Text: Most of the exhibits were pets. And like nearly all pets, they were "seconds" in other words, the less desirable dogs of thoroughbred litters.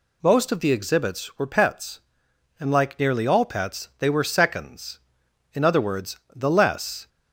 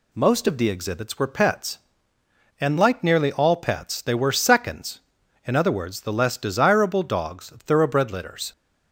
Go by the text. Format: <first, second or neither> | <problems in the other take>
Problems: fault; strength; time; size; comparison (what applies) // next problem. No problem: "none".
second | stops before "desirable dogs of thoroughbred litters"; at 7.0 s